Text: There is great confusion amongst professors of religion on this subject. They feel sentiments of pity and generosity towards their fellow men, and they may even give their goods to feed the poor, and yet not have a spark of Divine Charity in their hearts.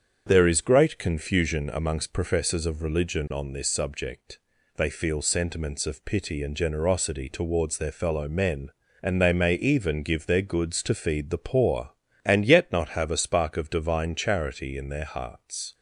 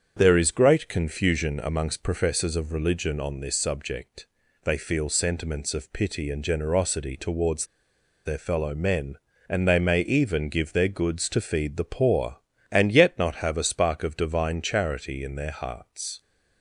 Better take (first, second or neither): first